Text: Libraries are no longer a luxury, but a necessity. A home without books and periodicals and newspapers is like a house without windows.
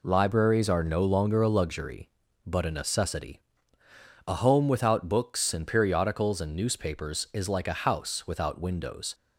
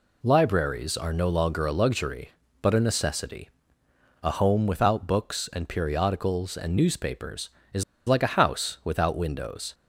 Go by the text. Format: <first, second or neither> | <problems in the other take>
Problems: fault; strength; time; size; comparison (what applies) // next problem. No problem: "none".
first | pauses between "is" and "like"; slight; at 7.8 s; 0.24 s long